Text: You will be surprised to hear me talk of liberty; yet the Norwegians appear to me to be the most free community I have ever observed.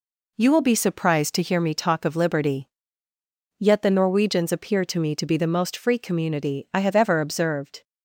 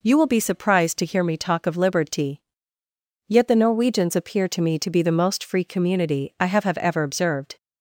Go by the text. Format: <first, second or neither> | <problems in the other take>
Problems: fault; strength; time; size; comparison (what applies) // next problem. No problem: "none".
first | says "have" twice; at 6.6 s